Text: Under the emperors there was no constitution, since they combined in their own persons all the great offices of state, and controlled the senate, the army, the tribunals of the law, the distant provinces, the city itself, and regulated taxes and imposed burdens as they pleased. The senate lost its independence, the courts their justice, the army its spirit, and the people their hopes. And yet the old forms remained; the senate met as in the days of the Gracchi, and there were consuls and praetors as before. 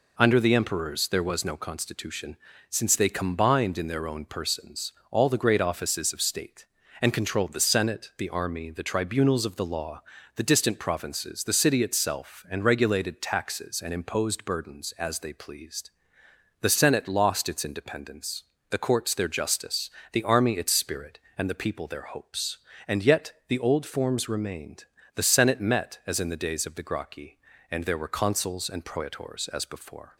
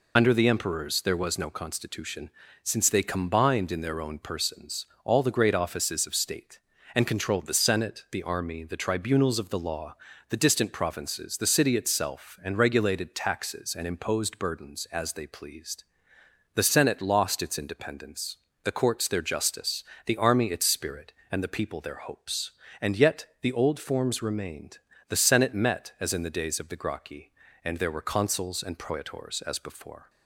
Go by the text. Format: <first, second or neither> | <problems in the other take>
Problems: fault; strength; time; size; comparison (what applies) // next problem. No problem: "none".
first | loses the start of "Under"; at 0.1 s; 35 ms // pauses between "persons" and "all"; slight; at 4.8 s; 0.18 s long; slight in the first